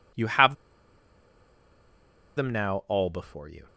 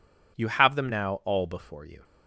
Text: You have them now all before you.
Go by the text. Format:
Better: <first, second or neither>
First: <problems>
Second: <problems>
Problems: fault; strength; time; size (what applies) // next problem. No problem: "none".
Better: second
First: pauses between "have" and "them"; strong; at 0.5 s; 1.8 s long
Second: none